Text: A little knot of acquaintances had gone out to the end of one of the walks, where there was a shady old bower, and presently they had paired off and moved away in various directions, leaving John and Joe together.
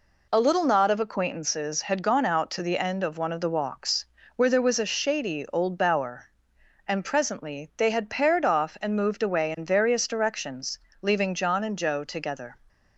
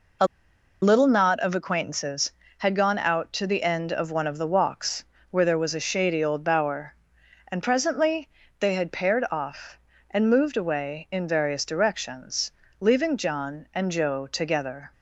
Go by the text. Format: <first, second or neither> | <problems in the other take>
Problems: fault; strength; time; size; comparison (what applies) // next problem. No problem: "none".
first | pauses between "A" and "little"; noticeable; at 0.2 s; 0.57 s long // pauses between "presently" and "they"; slight; at 8.2 s; 0.30 s long